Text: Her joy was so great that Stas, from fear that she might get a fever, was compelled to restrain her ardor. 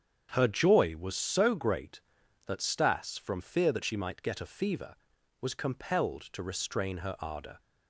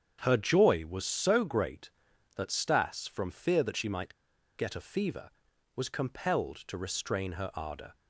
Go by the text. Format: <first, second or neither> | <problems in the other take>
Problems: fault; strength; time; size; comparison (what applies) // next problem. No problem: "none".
first | starts louder than the rest; strong; until 1.2 s; 7.5 dB; strong in the first // pauses between "might" and "get"; at 4.1 s; 0.43 s long